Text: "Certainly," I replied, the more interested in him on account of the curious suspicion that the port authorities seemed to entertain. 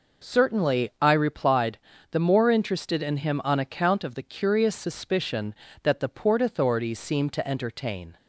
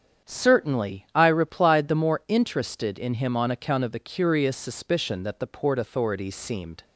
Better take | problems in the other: first | starts louder than the rest; strong; until 1.3 s; 8 dB // stops before "to entertain"; at 6.8 s

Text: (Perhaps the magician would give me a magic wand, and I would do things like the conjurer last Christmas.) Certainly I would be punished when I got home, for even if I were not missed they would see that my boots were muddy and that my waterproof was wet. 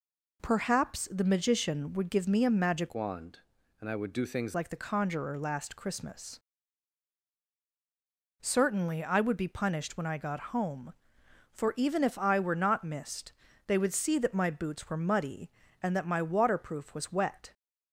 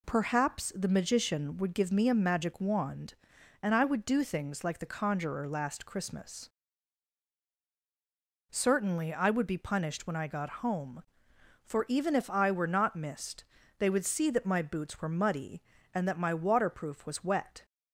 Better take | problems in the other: second | changes voice from "wand" to "things"; from 2.9 to 4.5 s; 1.6 s long // pauses between "missed" and "they"; slight; at 13.3 s; 0.36 s long; slight in the second

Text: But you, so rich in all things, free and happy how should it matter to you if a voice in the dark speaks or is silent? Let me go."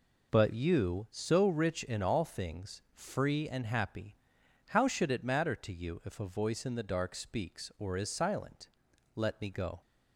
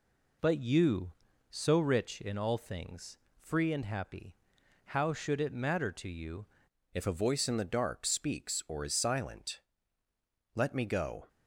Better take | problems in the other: first | pauses between "happy" and "how"; noticeable; at 4.3 s; 0.58 s long; noticeable in the first // changes voice at "if"; from 6.9 s on; 4.3 s long

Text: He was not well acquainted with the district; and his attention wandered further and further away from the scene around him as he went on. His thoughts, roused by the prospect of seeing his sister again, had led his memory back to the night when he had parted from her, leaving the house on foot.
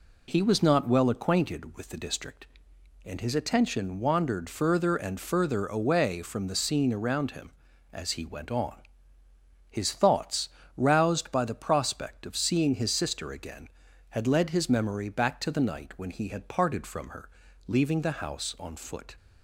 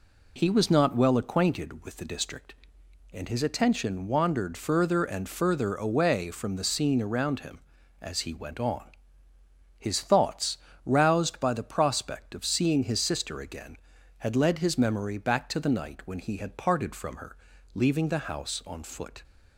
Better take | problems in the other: neither | none

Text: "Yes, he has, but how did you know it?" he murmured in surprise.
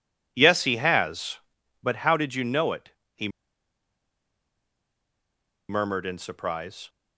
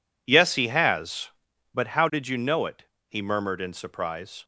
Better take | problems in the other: second | pauses between "he" and "murmured"; strong; at 3.2 s; 2.4 s long

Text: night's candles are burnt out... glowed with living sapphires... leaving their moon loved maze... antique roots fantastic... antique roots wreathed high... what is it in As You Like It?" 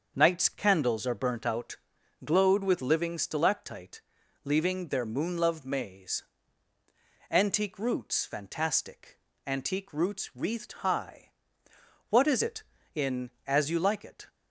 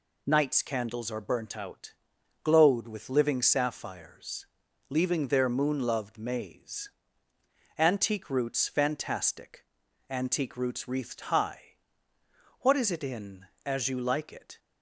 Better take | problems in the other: second | starts louder than the rest; until 1.1 s; 6.5 dB // says "stalactite" for "sapphires"; at 3.1 s

